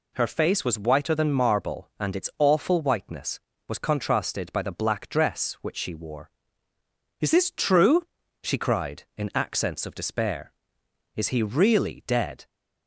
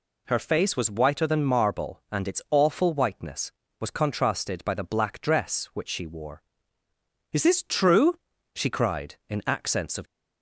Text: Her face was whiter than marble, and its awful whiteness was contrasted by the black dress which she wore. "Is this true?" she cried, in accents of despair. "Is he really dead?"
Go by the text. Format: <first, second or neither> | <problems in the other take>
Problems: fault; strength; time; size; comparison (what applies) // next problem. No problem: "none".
first | stops before "despair Is he really dead"; at 10.0 s